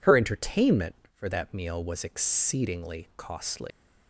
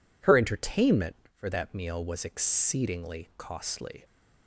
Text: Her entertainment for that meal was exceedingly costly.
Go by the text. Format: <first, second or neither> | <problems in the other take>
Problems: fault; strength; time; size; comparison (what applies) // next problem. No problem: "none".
second | leaves "costly" unfinished; at 3.7 s; 135 ms